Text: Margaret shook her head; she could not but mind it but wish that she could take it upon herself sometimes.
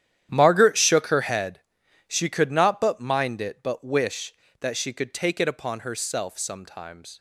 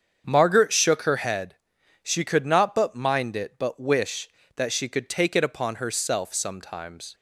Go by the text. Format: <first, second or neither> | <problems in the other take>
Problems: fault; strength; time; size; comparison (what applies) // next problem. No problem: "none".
second | gets quieter; strong; throughout; 15.5 dB // starts louder than the rest; strong; until 1.3 s; 10.5 dB; strong in the second